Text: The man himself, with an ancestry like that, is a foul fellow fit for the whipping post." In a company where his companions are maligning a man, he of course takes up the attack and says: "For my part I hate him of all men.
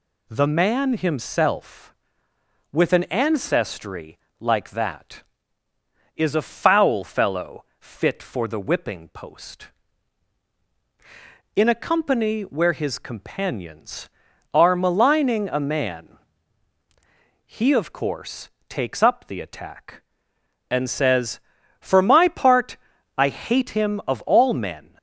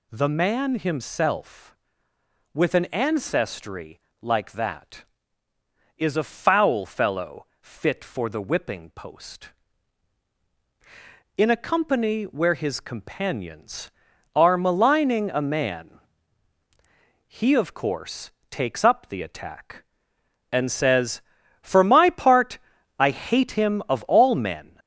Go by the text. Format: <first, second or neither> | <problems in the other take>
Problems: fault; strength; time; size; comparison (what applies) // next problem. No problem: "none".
first | gets louder; noticeable; throughout; 4 dB // pauses between "ancestry" and "like"; slight; at 3.9 s; 0.24 s long; slight in the first // pauses between "fellow" and "fit"; slight; at 7.4 s; 0.16 s long; slight in the first // pauses between "course" and "takes"; slight; at 18.3 s; 0.20 s long; slight in the first // pauses between "part" and "I"; at 22.5 s; 0.42 s long; also in the first